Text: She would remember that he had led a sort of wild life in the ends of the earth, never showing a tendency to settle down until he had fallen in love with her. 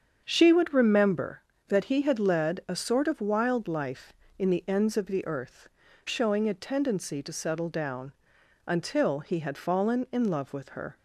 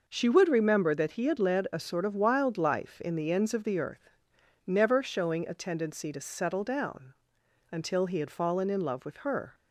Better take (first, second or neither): second